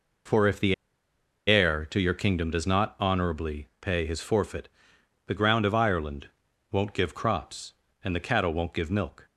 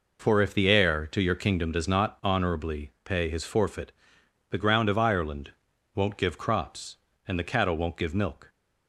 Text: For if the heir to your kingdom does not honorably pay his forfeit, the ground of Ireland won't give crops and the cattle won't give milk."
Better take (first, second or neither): second